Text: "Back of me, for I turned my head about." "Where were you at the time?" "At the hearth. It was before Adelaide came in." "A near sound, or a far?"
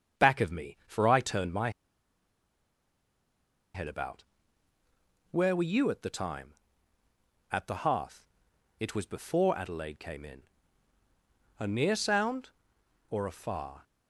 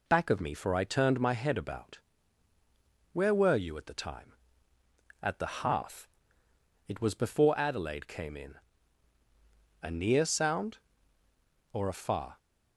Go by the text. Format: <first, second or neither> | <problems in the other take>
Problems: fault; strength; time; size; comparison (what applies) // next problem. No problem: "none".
second | starts louder than the rest; strong; until 1.2 s; 7 dB // pauses between "my" and "head"; strong; at 1.6 s; 2.0 s long